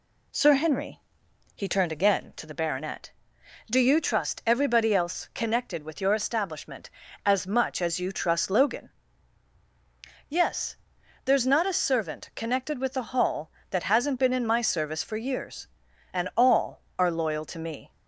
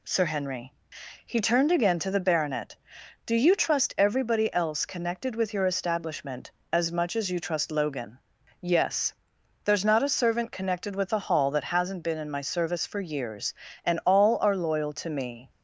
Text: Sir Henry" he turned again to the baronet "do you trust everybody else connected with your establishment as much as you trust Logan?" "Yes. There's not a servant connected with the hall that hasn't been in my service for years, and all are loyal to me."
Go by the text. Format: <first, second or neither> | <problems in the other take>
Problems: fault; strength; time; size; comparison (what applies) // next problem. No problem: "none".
neither | pauses between "Henry" and "he"; noticeable; the same in both